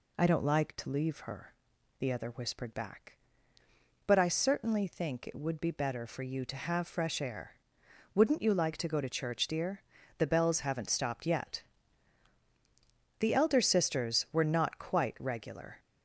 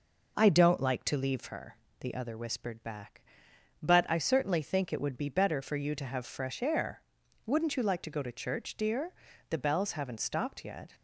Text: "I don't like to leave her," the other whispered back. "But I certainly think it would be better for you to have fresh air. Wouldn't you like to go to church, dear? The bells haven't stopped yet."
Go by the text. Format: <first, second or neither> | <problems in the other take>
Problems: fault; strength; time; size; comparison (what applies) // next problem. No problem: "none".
second | goes on to say "The elder sisters were not quite regular"; strong; from 13.2 s on; 2.5 s long